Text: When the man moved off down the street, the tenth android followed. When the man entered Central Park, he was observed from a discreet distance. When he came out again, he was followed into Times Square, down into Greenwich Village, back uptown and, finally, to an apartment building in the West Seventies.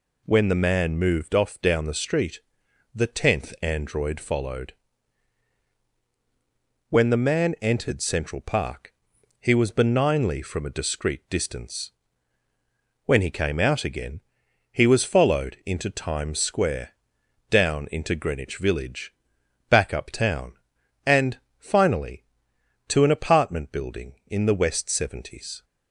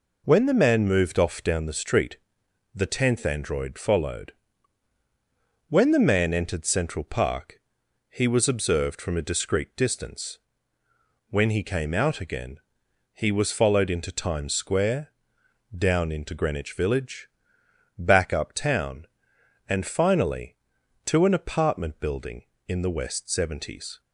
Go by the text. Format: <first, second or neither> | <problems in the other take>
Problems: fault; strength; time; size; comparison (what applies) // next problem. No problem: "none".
second | says "benignly" for "observed"; at 9.7 s